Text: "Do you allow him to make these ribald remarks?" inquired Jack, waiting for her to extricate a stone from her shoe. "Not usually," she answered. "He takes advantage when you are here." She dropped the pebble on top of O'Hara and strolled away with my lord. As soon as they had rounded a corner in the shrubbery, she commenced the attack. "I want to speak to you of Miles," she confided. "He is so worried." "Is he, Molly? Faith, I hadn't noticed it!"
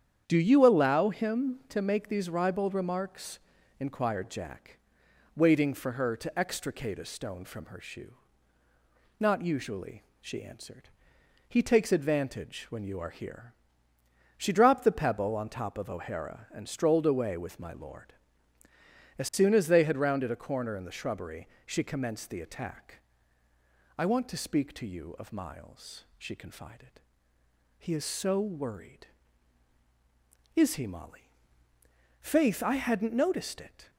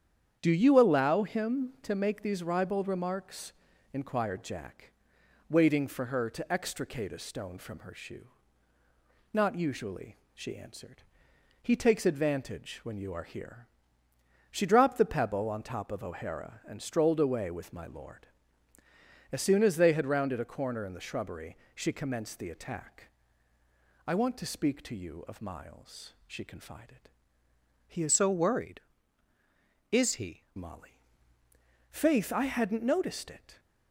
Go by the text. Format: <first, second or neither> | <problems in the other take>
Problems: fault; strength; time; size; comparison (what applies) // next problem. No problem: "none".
first | starts louder than the rest; strong; until 1.4 s; 8.5 dB; strong in the first // changes voice from "so" to "he"; from 28.1 to 30.4 s; 2.3 s long